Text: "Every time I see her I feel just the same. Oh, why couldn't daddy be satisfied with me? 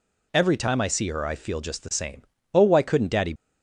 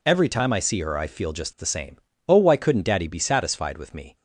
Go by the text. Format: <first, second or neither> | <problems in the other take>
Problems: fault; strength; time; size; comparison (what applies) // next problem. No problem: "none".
second | stops before "be satisfied with me"; at 3.3 s